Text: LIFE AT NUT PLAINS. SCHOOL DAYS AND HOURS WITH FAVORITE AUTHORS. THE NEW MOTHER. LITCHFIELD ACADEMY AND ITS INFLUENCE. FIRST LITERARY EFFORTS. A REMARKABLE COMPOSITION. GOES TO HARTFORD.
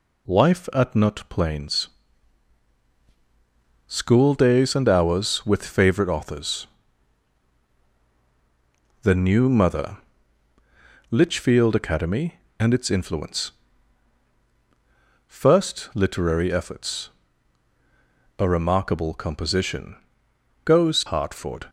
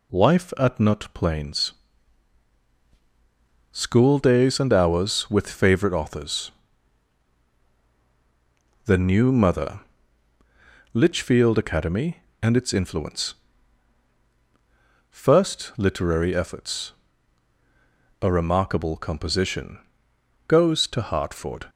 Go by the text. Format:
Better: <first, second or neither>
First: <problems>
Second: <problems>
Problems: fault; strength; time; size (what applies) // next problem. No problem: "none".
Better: second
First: skips "TO"; at 21.0 s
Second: none